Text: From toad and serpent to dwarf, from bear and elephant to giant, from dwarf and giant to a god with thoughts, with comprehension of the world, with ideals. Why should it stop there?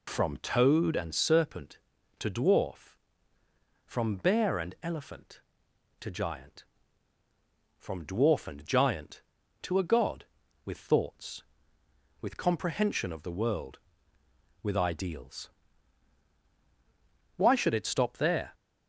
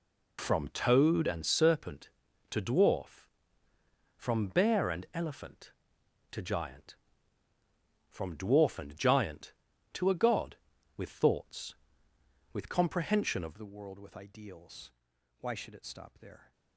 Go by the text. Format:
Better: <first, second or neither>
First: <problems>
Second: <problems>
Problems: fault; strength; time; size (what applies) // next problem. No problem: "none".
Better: first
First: none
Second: changes voice at "the"; from 13.5 s on; 3.0 s long